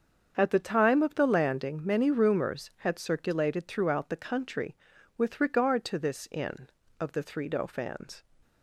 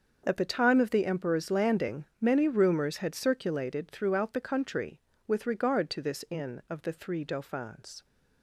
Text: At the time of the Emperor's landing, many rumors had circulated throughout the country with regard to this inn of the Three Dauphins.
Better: second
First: starts louder than the rest; strong; until 1.3 s; 7 dB // skips "Emperor's"; at 1.2 s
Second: starts louder than the rest; until 1.2 s; 6.5 dB

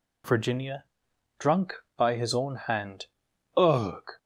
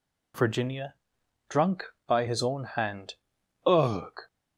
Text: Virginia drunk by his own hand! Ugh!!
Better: neither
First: pauses between "Virginia" and "drunk"; noticeable; at 0.8 s; 0.52 s long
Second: pauses between "Virginia" and "drunk"; noticeable; at 0.9 s; 0.52 s long

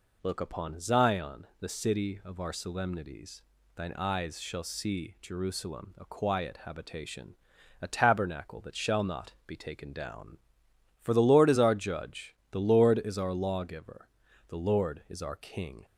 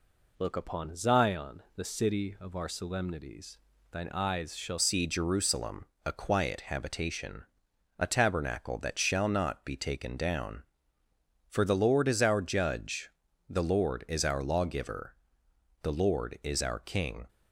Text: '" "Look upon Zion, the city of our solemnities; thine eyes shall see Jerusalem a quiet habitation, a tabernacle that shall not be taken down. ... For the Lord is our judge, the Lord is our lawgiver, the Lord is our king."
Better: first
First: none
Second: changes voice at "see"; from 4.7 s on; 12.5 s long // pauses between "Jerusalem" and "a"; slight; at 5.8 s; 0.22 s long

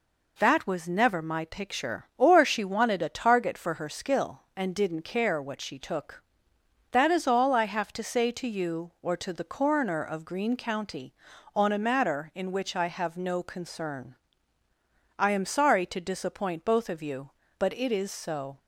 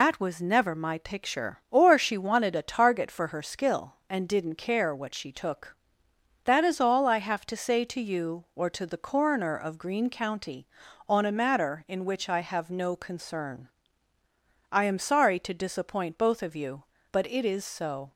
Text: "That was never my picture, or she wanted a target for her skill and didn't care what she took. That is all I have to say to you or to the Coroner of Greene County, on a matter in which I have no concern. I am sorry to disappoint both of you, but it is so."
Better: first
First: none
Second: loses the start of "That"; at 0.0 s; 95 ms

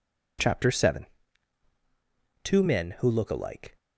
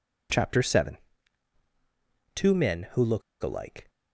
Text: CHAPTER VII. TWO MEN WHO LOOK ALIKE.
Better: first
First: none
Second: pauses between "LOOK" and "ALIKE"; slight; at 3.2 s; 0.21 s long

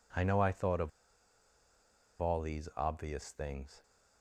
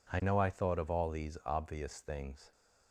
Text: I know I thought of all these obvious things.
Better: second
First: pauses between "of" and "all"; strong; at 0.9 s; 1.3 s long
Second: none

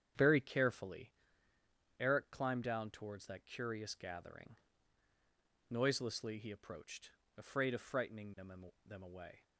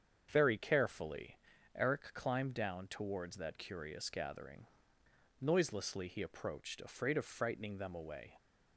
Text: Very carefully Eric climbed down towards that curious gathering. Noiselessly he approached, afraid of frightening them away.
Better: second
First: starts louder than the rest; strong; until 2.0 s; 8.5 dB // pauses between "carefully" and "Eric"; noticeable; at 1.1 s; 0.90 s long // says "them" twice; at 8.8 s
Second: starts louder than the rest; strong; until 1.3 s; 7.5 dB // pauses between "carefully" and "Eric"; at 1.3 s; 0.38 s long

